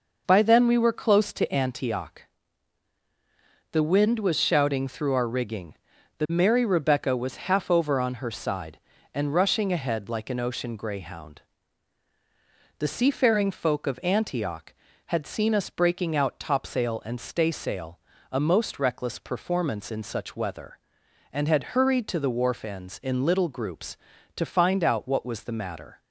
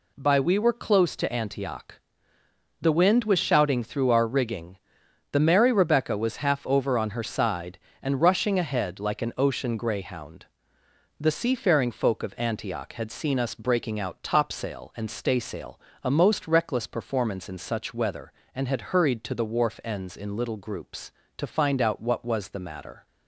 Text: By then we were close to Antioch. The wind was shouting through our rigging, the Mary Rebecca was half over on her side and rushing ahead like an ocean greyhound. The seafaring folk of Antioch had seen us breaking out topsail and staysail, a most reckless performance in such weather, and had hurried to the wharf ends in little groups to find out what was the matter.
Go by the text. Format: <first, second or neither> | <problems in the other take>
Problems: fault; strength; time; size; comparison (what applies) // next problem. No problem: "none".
first | skips "then"; at 0.3 s